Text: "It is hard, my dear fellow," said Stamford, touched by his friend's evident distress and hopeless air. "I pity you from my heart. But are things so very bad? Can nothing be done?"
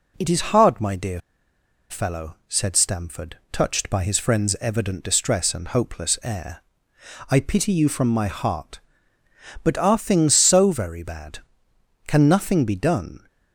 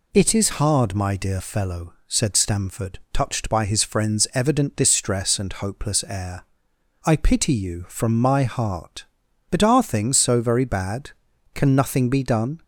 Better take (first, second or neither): second